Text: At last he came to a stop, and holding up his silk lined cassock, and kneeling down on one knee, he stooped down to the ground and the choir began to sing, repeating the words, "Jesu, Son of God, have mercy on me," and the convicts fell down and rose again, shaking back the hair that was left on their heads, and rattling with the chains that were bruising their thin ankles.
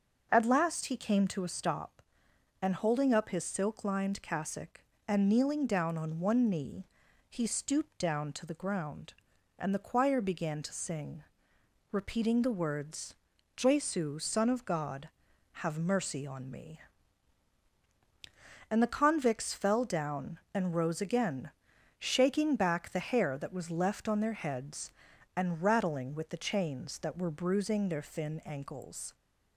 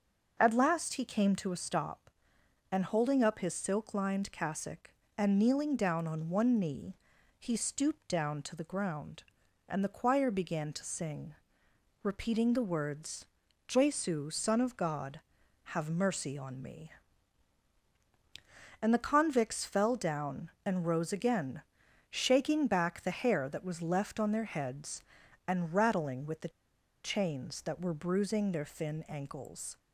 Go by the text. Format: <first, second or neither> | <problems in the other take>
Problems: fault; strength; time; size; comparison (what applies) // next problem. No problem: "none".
first | starts louder than the rest; noticeable; until 1.4 s; 6 dB // pauses between "the" and "chains"; noticeable; at 26.5 s; 0.53 s long